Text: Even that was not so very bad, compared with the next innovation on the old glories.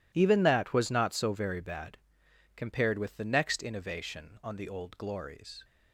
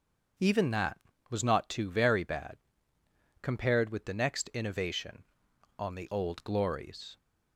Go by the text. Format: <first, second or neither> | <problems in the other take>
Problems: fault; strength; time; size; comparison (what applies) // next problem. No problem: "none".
first | starts louder than the rest; until 1.7 s; 6.5 dB // says "too" for "so"; at 1.6 s